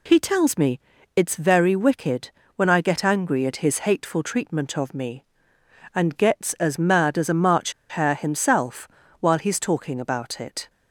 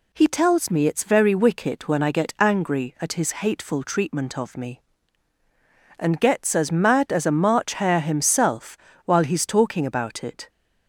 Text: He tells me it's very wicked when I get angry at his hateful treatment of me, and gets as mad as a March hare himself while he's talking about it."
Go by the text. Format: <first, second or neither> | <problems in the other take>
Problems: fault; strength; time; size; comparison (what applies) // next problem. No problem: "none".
second | pauses between "me" and "it's"; at 0.7 s; 0.38 s long // pauses between "wicked" and "when"; slight; at 2.3 s; 0.24 s long // pauses between "March" and "hare"; slight; at 7.7 s; 0.17 s long // pauses between "himself" and "while"; slight; at 8.8 s; 0.32 s long; slight in the second